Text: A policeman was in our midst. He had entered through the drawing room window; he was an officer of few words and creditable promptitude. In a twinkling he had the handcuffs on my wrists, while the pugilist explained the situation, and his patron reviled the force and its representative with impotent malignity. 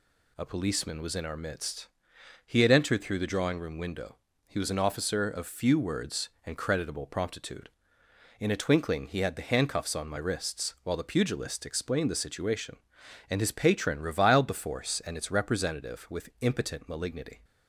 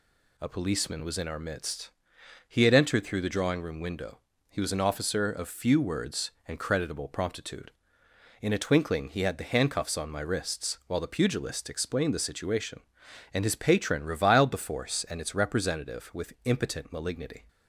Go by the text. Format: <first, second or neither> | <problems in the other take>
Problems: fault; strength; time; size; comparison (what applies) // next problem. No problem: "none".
neither | none